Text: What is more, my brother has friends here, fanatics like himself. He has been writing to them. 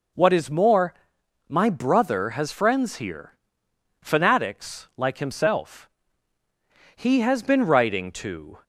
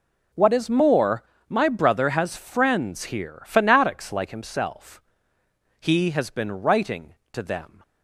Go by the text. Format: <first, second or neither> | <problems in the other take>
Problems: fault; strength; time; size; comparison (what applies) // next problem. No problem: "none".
second | stops before "them"; at 8.6 s